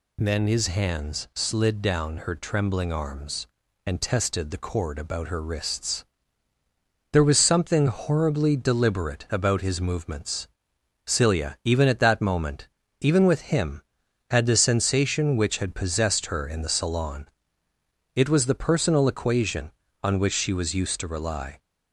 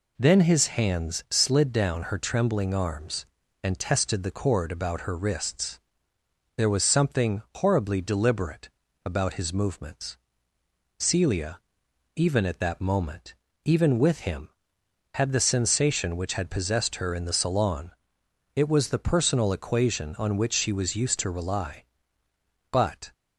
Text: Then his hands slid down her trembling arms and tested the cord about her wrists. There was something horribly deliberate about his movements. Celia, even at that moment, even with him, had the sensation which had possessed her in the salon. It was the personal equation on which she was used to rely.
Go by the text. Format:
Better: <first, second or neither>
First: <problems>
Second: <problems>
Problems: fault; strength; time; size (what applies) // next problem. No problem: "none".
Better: first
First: none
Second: pauses between "deliberate" and "about"; slight; at 8.6 s; 0.34 s long // goes on to say "But"; slight; from 22.7 s on; 0.42 s long